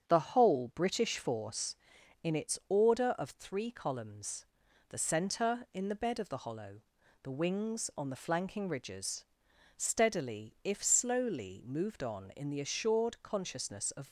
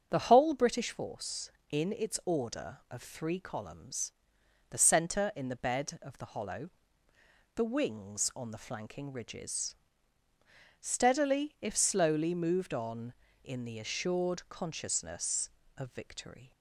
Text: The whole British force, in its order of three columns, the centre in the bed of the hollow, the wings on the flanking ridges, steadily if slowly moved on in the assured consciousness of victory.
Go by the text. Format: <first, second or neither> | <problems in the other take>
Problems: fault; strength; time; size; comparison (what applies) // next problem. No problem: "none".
second | starts louder than the rest; strong; until 1.0 s; 7.5 dB; also in the second // stops before "victory"; at 14.0 s